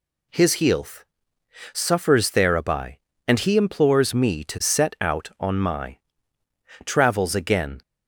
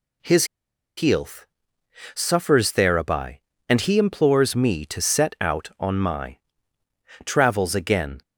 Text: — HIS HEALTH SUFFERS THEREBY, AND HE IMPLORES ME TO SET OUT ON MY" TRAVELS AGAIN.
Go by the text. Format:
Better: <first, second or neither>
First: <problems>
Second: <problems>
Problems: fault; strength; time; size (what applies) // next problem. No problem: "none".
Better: first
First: pauses between "HEALTH" and "SUFFERS"; noticeable; at 1.0 s; 0.70 s long // pauses between "MY" and "TRAVELS"; noticeable; at 5.9 s; 0.88 s long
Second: pauses between "HIS" and "HEALTH"; noticeable; at 0.4 s; 0.52 s long // pauses between "HEALTH" and "SUFFERS"; noticeable; at 1.4 s; 0.70 s long // pauses between "MY" and "TRAVELS"; noticeable; at 6.3 s; 0.88 s long